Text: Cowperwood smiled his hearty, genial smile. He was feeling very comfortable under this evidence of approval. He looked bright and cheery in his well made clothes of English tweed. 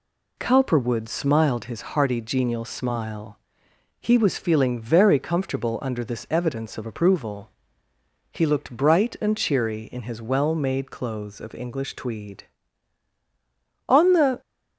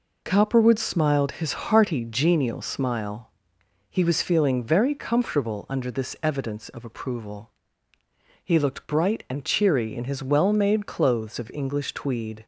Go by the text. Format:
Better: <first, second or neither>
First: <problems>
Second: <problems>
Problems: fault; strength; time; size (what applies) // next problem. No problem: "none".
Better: second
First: goes on to say "On the"; from 13.8 s on; 0.52 s long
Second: none